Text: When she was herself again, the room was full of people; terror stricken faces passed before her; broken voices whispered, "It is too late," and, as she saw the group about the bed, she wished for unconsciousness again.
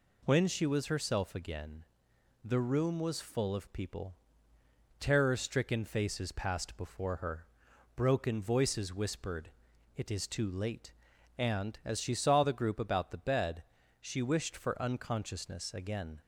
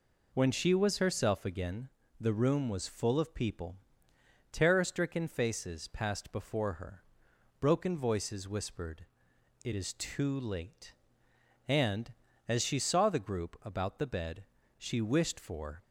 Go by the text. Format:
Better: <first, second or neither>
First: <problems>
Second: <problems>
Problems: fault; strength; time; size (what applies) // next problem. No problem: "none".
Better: first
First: none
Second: stops before "unconsciousness again"; at 15.8 s